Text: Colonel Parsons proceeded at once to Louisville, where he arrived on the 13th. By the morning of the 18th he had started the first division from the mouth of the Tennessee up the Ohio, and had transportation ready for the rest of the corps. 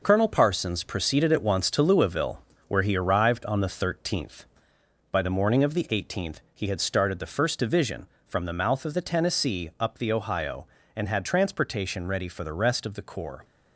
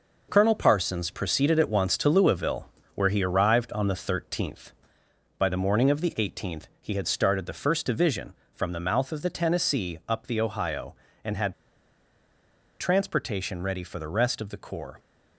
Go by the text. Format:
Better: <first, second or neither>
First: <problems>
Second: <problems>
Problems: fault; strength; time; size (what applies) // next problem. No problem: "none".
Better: first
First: none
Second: pauses between "had" and "transportation"; strong; at 11.5 s; 1.2 s long